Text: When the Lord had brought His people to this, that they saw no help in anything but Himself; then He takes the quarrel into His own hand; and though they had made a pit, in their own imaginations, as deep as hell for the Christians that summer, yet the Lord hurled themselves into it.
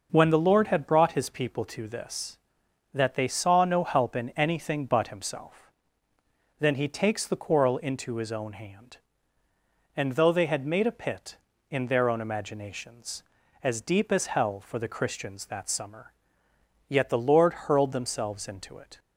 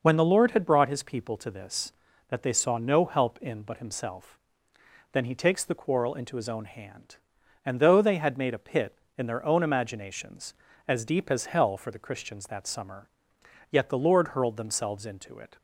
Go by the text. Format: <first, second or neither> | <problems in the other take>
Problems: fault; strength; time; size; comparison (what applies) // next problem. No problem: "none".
first | skips "anything"; at 3.6 s